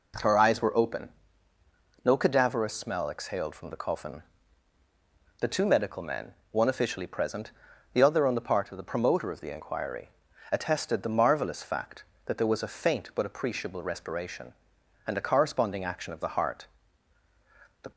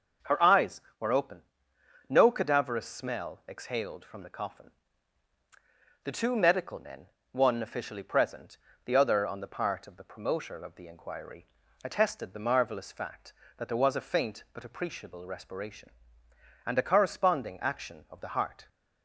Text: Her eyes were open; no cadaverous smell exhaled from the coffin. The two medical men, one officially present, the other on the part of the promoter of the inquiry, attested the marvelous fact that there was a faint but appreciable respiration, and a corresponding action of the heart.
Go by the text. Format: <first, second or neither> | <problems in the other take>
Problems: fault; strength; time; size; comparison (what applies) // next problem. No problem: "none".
second | goes on to say "The"; slight; from 17.8 s on; 0.08 s long